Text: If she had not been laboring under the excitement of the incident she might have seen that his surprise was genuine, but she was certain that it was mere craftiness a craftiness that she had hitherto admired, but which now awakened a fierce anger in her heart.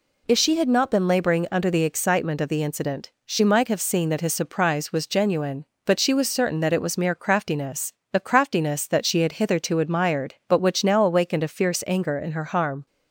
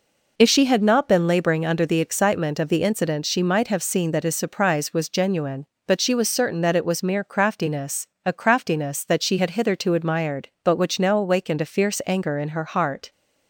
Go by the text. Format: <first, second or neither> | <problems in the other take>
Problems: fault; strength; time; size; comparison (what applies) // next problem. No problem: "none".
second | pauses between "craftiness" and "a"; slight; at 7.9 s; 0.22 s long; slight in the second // says "harm" for "heart"; at 12.4 s